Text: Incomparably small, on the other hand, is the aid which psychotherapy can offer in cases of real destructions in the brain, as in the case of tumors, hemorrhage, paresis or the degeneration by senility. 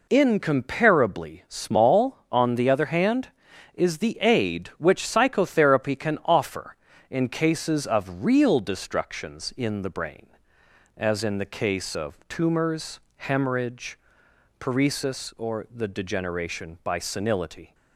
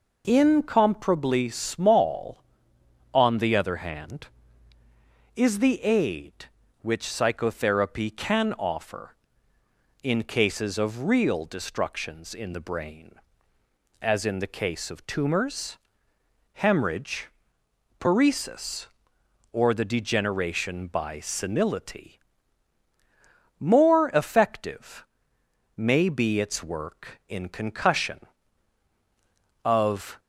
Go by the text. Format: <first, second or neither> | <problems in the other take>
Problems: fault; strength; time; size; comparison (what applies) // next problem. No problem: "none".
first | goes on to say "More effective may be its work in concussion of"; strong; from 23.5 s on; 6.6 s long